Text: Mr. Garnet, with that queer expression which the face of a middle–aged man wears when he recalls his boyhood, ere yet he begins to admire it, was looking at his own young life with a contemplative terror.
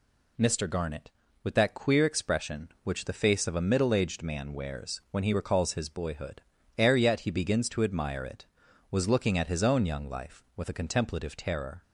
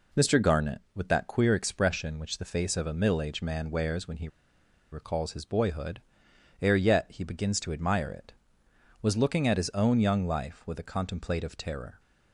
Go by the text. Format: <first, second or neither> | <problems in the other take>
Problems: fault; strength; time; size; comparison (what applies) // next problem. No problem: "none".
first | pauses between "he" and "recalls"; noticeable; at 4.2 s; 0.64 s long